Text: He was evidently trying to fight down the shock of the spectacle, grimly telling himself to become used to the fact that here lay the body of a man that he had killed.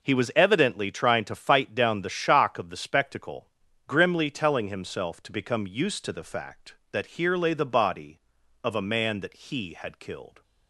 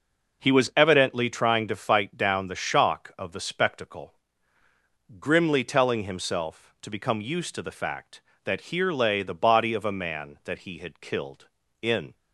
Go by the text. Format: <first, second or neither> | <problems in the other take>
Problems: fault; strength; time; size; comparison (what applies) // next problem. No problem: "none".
first | goes on to say "In"; slight; from 11.8 s on; 0.32 s long